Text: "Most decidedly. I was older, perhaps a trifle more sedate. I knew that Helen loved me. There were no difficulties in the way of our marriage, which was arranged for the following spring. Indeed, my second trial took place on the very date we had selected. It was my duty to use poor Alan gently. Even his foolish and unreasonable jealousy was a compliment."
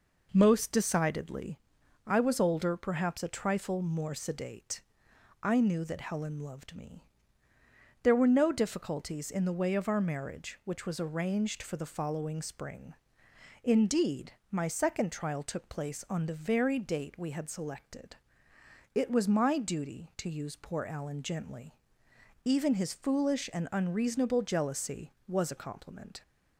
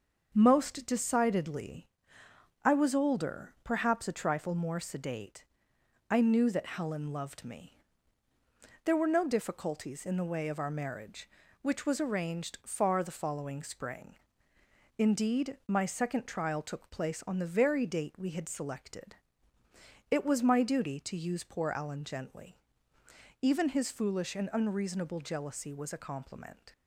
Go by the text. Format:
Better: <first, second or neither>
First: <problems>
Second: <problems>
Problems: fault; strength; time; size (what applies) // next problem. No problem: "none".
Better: first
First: none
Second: starts louder than the rest; until 1.3 s; 6.5 dB // says "far" for "for"; at 12.6 s